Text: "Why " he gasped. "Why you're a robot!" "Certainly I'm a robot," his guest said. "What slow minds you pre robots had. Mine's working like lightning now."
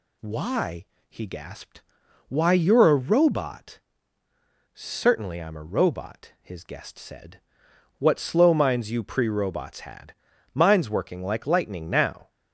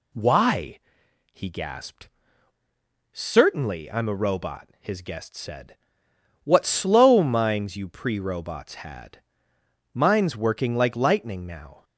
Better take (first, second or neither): first